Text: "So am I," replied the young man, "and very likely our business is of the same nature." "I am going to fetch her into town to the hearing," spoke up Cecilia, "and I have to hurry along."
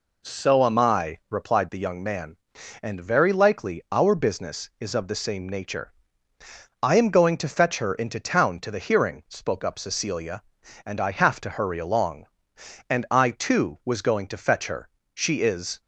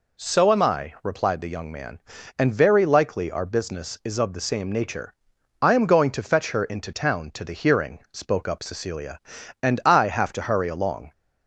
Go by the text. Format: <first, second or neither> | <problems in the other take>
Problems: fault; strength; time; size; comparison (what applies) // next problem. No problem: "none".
second | goes on to say "And I too was going to fetch her She is"; strong; from 12.8 s on; 2.9 s long